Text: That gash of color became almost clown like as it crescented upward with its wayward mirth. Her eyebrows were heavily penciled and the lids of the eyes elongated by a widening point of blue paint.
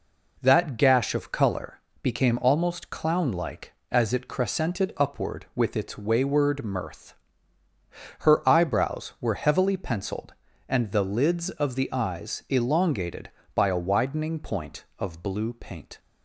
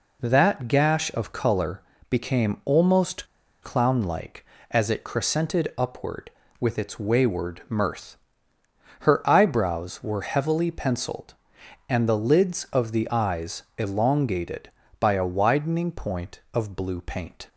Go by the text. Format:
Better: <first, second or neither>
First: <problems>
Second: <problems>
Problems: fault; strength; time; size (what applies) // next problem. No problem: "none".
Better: first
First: pauses between "color" and "became"; slight; at 1.8 s; 0.20 s long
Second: pauses between "color" and "became"; slight; at 1.8 s; 0.30 s long // pauses between "almost" and "clown"; slight; at 3.2 s; 0.35 s long